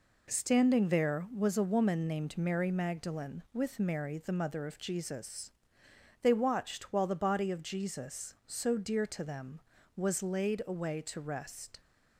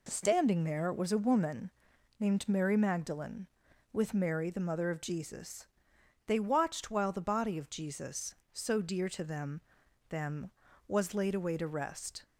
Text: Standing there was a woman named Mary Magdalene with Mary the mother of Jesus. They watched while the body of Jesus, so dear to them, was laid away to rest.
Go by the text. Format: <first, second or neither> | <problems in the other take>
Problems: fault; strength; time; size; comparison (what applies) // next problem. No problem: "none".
first | pauses between "woman" and "named"; noticeable; at 1.6 s; 0.48 s long // says "them" twice; at 10.0 s